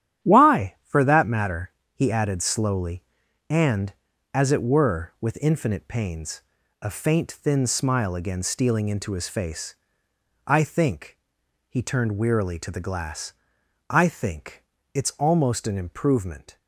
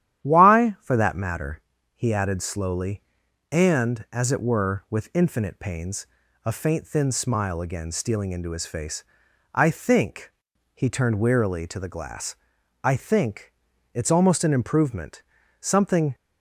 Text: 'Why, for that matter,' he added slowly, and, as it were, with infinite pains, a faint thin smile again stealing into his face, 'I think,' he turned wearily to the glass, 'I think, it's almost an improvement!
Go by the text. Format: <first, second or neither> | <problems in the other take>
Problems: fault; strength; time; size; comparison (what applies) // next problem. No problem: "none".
first | starts louder than the rest; strong; until 1.2 s; 11 dB; strong in the first // goes on to say "Something"; from 15.5 s on; 0.56 s long